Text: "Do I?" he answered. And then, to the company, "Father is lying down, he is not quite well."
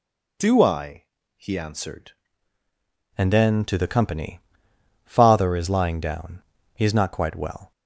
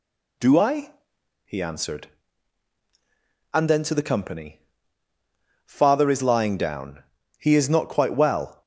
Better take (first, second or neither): second